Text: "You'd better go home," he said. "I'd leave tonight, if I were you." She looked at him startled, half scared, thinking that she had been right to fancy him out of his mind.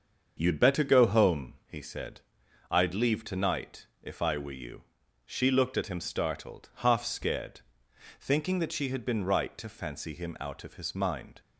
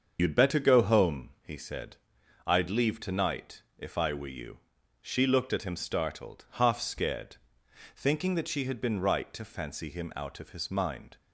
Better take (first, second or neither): first